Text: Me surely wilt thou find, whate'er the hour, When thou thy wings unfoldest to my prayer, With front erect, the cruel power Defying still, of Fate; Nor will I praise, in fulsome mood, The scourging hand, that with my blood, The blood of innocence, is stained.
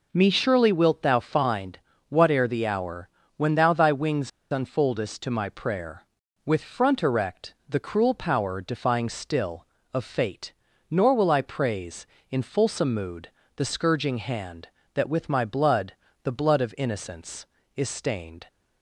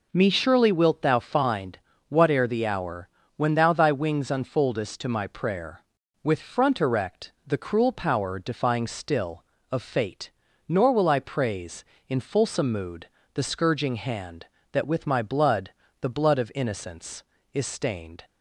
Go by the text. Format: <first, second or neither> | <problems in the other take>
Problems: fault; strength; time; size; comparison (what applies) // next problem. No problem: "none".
second | pauses between "wings" and "unfoldest"; slight; at 4.2 s; 0.22 s long